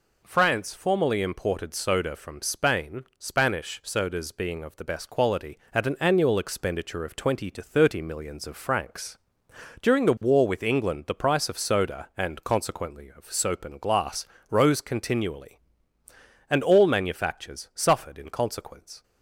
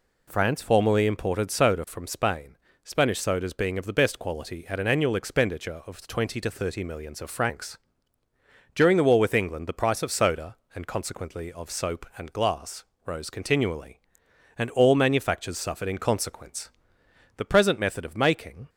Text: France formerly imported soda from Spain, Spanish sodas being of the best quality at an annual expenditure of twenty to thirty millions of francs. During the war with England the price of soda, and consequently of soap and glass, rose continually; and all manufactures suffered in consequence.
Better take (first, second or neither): first